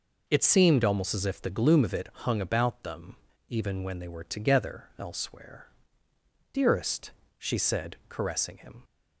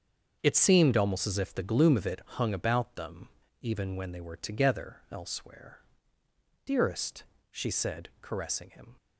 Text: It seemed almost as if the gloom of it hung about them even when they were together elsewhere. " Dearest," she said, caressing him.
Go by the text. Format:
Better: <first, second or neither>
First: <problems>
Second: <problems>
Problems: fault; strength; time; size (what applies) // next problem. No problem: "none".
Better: first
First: pauses between "them" and "even"; slight; at 3.1 s; 0.32 s long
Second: gets quieter; strong; throughout; 15.5 dB // pauses between "them" and "even"; slight; at 3.2 s; 0.32 s long